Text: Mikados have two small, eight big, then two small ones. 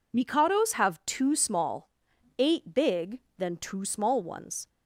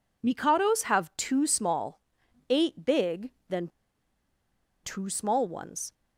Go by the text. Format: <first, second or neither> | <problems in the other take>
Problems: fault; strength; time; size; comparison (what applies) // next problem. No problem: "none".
first | pauses between "then" and "two"; at 3.6 s; 1.1 s long